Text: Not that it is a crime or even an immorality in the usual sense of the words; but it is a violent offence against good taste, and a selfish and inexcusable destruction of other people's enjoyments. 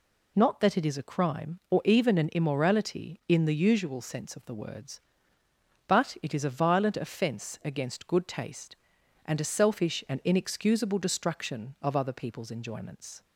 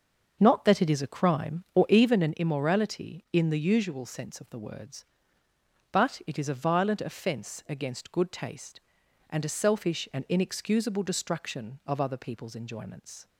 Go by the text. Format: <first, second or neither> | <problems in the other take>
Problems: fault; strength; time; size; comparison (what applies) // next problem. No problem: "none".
first | starts louder than the rest; until 2.3 s; 6.5 dB